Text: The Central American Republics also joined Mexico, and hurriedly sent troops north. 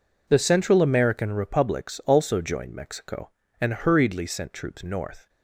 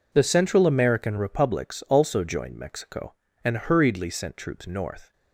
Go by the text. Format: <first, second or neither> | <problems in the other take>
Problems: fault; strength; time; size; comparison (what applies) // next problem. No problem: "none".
neither | none